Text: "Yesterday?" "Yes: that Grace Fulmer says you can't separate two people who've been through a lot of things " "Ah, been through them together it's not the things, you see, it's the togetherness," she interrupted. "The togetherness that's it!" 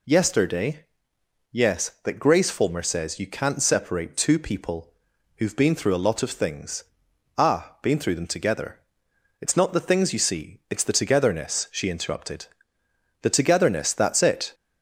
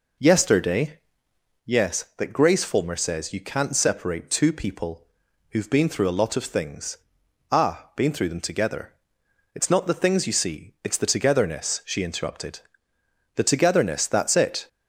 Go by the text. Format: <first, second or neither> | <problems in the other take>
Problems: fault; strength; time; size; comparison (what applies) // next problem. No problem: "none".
first | starts louder than the rest; noticeable; until 1.7 s; 5 dB // pauses between "people" and "who've"; at 5.0 s; 0.42 s long; also in the first // pauses between "together" and "it's"; noticeable; at 8.9 s; 0.62 s long; noticeable in the first